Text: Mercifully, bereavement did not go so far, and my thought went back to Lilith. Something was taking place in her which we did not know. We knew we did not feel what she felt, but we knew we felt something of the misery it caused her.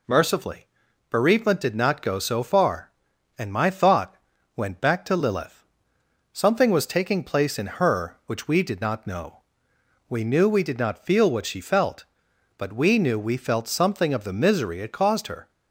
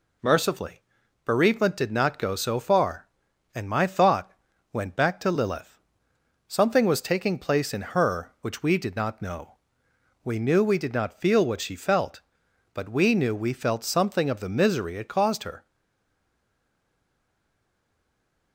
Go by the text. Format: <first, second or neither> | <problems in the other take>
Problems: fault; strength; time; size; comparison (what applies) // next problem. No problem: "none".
first | pauses between "thought" and "went"; at 4.3 s; 0.40 s long; also in the first // stays silent after the last word; strong; from 15.6 s on; 2.9 s long